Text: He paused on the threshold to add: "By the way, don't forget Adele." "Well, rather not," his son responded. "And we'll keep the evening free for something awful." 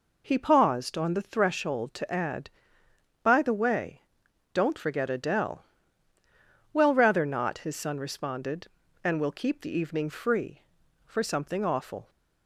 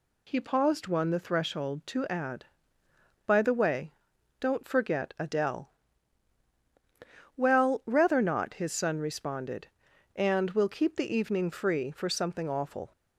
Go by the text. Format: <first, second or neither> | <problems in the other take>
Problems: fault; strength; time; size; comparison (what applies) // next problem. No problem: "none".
first | says "one" for "on"; at 0.8 s